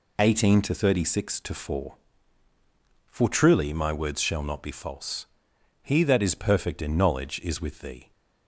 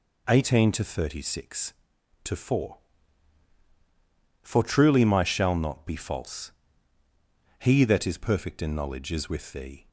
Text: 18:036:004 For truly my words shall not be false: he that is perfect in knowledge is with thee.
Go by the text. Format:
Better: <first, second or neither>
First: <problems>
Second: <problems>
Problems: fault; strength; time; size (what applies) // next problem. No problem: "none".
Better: first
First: none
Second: skips "words"; at 5.2 s